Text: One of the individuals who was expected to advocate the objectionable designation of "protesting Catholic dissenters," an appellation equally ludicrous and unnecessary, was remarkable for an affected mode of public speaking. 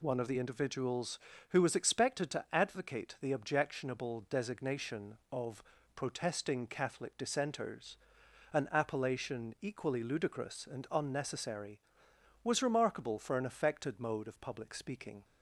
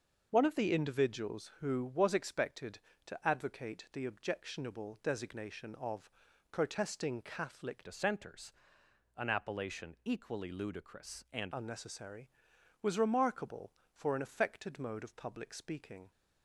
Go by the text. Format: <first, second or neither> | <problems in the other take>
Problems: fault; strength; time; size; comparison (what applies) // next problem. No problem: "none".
first | starts louder than the rest; until 1.3 s; 6 dB // pauses between "of" and "protesting"; at 6.1 s; 0.40 s long; slight in the first // changes voice from "dissenters" to "and"; from 7.8 to 11.5 s; 3.7 s long